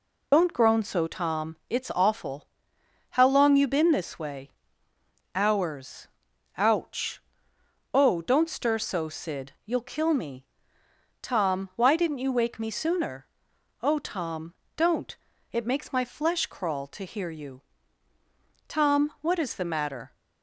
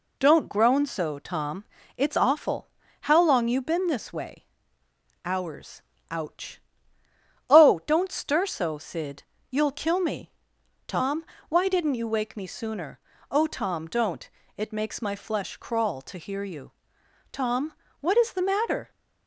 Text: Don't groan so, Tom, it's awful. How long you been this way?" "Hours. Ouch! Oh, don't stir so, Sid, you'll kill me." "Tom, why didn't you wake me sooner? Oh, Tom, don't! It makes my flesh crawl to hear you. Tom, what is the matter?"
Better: second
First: loses the start of "Don't"; at 0.3 s; 70 ms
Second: none

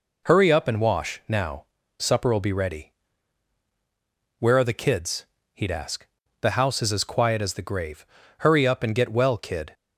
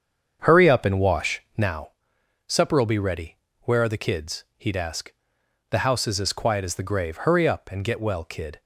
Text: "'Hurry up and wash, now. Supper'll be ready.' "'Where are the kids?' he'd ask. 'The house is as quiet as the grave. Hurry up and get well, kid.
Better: first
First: none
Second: starts louder than the rest; strong; until 1.8 s; 7.5 dB

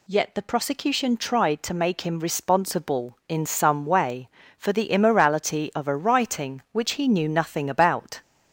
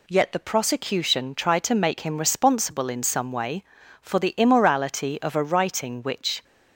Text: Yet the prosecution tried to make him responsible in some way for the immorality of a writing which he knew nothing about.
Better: first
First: none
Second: stops before "he knew nothing about"; at 6.4 s

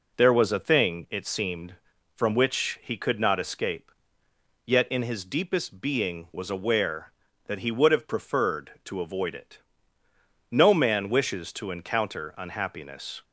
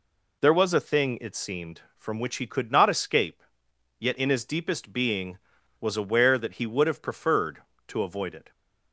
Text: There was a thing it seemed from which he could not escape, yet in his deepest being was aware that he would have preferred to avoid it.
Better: second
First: goes on to say "No man wishes to encounter unhappiness"; strong; from 10.5 s on; 2.7 s long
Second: none

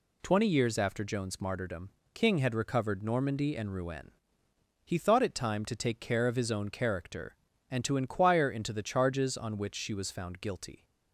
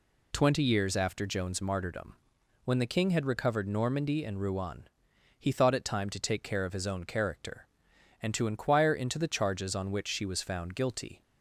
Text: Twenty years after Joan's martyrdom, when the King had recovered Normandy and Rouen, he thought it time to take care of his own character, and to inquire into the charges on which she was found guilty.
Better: second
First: skips "when the"; at 2.0 s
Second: none

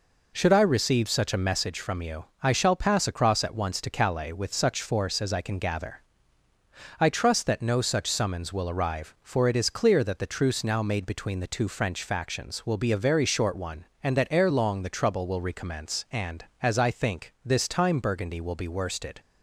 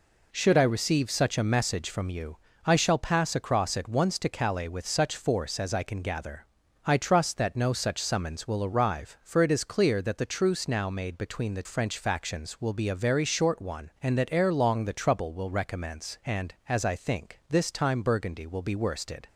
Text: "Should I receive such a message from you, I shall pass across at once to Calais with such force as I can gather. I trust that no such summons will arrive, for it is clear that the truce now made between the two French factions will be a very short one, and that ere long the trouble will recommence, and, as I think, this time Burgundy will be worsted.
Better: first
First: none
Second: skips "two"; at 11.6 s

